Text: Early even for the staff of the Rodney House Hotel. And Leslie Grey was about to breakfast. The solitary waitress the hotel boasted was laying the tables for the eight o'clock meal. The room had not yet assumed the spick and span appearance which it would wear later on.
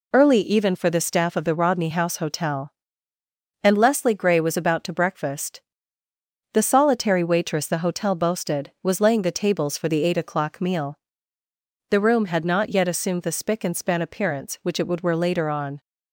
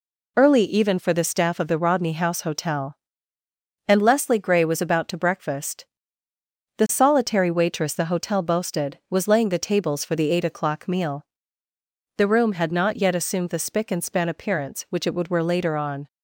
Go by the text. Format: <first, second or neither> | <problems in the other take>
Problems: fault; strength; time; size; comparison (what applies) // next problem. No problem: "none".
neither | none